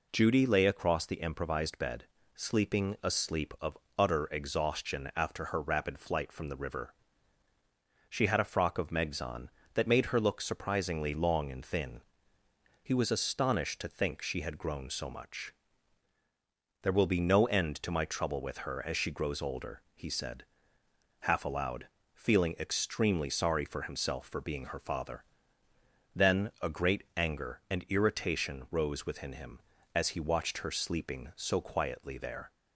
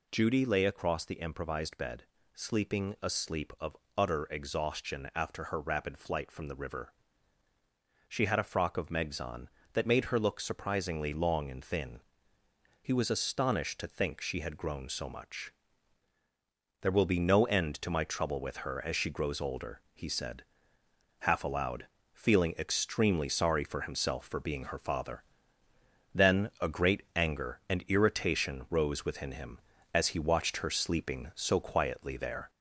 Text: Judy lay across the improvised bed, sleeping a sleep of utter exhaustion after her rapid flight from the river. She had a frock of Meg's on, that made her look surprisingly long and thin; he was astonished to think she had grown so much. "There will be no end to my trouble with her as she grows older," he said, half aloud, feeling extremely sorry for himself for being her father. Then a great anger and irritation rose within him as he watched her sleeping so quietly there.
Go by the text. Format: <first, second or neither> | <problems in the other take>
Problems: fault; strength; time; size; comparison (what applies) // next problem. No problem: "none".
first | gets louder; slight; throughout; 2.5 dB // pauses between "of" and "utter"; slight; at 3.7 s; 0.20 s long; slight in the first